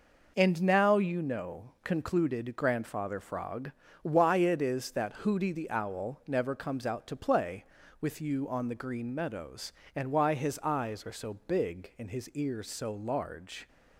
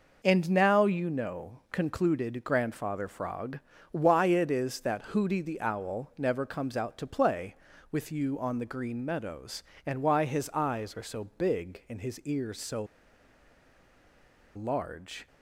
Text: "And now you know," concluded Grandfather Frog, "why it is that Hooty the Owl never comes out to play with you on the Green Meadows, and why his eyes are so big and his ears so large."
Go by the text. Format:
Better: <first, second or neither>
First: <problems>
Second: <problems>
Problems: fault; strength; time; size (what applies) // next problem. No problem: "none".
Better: first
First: none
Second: pauses between "so" and "large"; strong; at 12.8 s; 1.7 s long